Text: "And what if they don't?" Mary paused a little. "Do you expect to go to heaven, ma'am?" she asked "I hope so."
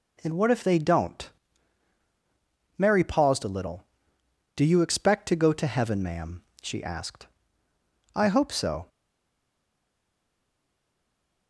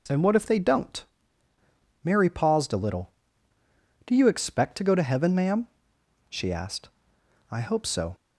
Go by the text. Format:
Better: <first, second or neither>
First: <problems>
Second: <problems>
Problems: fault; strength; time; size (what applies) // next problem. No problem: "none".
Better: second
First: pauses between "asked" and "I"; noticeable; at 7.2 s; 0.88 s long // stays silent after the last word; strong; from 8.8 s on; 2.6 s long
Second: pauses between "asked" and "I"; noticeable; at 6.8 s; 0.62 s long